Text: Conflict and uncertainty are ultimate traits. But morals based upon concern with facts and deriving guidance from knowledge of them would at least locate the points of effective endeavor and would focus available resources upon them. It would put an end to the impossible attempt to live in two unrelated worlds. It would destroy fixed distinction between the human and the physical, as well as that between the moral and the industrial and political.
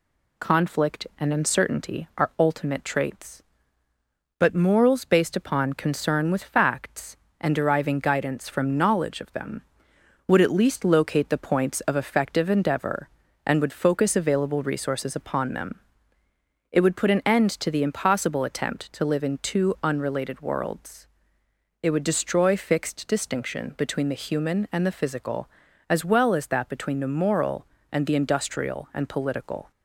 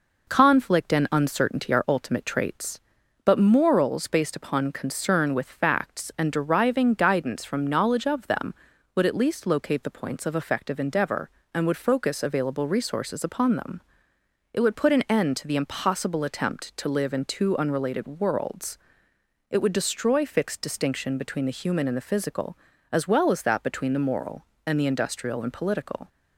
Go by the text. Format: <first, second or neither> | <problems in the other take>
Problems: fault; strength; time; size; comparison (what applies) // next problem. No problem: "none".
neither | none